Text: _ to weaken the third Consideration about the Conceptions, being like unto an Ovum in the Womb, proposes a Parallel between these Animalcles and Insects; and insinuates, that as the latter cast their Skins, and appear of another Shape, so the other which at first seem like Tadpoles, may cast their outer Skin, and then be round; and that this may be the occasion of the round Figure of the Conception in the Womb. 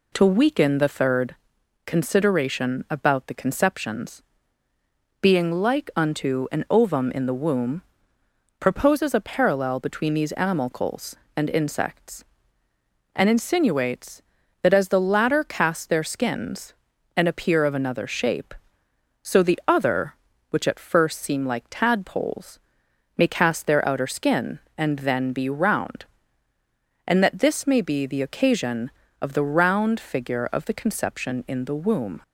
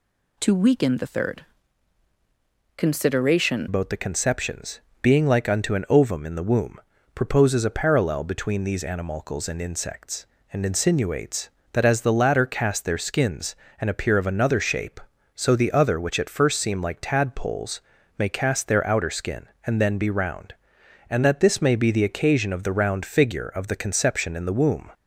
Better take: first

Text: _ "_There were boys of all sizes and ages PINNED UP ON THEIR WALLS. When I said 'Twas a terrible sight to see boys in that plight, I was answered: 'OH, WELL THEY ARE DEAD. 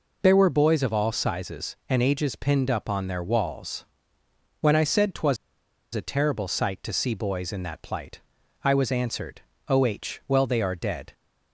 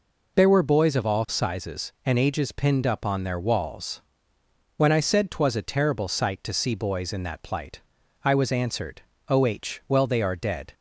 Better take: second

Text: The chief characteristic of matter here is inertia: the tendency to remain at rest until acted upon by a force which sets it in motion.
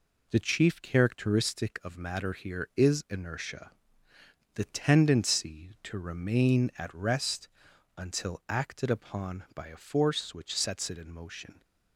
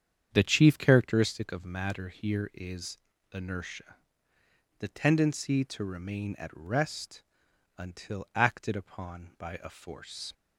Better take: first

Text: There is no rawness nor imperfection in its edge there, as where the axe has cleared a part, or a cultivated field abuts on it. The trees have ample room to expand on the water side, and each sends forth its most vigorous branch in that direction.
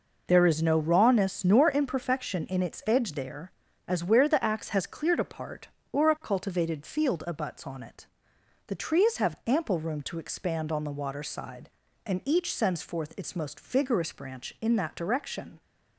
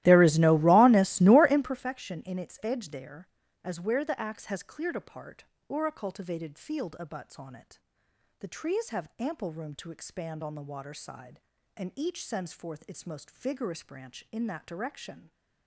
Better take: first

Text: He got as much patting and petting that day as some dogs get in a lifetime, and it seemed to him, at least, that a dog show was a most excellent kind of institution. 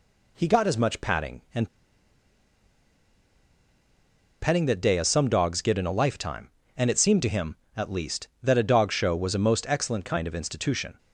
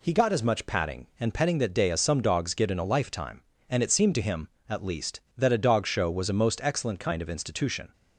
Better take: second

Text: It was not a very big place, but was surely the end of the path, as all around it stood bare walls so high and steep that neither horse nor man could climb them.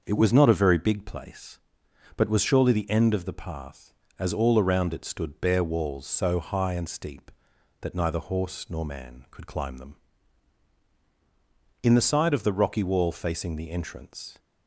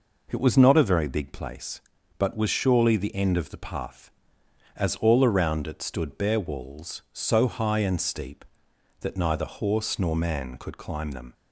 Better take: second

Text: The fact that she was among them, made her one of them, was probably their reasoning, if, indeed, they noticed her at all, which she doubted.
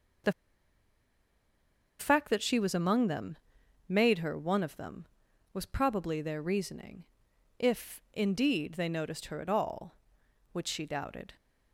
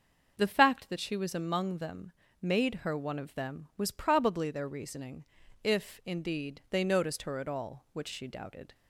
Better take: second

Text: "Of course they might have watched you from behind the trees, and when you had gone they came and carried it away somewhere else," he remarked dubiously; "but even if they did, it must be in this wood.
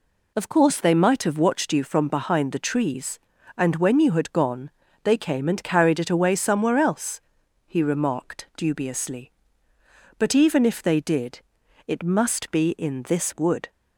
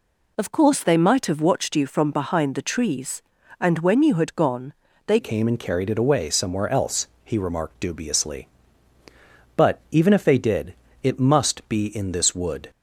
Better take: first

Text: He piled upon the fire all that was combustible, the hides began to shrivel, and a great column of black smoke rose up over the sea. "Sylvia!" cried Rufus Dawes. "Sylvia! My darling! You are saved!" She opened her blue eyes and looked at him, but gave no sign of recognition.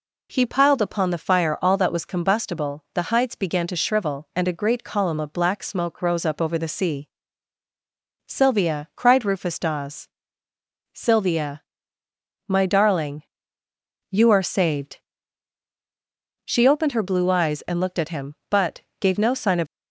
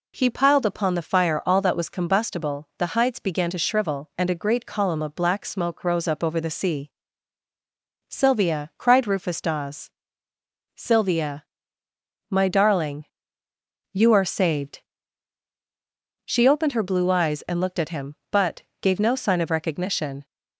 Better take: second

